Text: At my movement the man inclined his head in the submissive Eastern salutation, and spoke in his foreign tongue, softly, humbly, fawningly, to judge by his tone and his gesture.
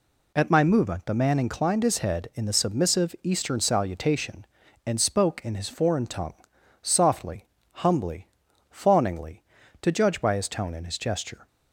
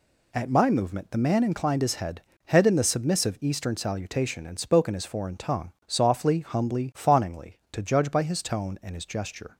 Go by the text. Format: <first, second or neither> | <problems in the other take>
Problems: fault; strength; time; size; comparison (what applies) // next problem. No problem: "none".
first | says "head" twice; at 2.4 s